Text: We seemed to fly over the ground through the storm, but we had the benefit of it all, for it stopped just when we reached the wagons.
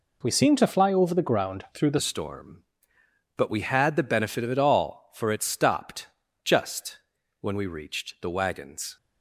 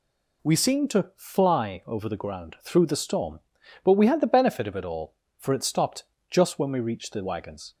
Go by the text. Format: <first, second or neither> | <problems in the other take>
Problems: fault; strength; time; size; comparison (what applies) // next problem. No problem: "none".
second | changes voice at "storm"; from 2.0 s on; 6.9 s long // pauses between "stopped" and "just"; slight; at 6.0 s; 0.36 s long; slight in the second // pauses between "just" and "when"; at 6.9 s; 0.42 s long